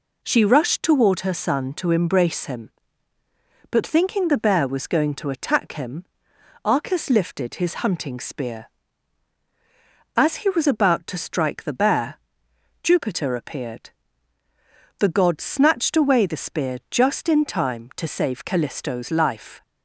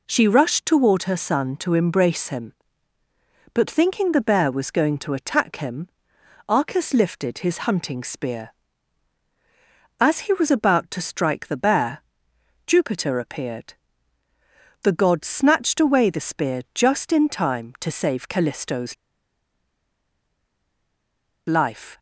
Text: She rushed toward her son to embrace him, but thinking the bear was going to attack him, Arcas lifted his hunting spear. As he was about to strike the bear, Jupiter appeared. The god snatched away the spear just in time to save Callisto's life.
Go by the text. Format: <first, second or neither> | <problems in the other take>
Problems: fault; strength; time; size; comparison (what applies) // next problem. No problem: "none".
first | pauses between "Callisto's" and "life"; strong; at 18.9 s; 2.5 s long